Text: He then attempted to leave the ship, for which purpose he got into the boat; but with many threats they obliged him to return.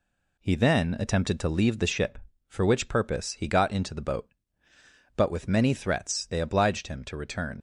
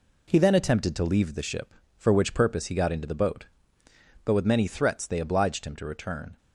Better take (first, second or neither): second